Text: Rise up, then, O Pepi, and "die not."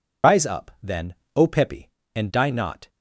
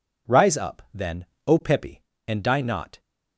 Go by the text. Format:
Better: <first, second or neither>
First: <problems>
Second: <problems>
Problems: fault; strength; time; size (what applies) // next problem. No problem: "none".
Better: second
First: loses the start of "Rise"; at 0.2 s; 80 ms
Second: none